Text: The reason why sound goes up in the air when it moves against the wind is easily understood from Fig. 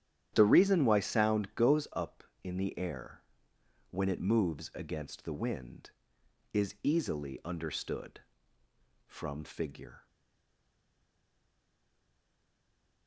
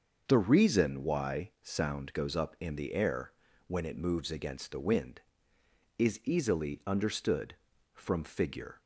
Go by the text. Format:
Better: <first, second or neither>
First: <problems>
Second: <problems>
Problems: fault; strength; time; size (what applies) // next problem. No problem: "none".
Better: second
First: starts louder than the rest; strong; until 1.3 s; 10.5 dB // pauses between "air" and "when"; noticeable; at 3.2 s; 0.70 s long // stays silent after the last word; strong; from 10.0 s on; 3.0 s long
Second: starts louder than the rest; until 1.3 s; 6.5 dB // pauses between "air" and "when"; slight; at 3.3 s; 0.36 s long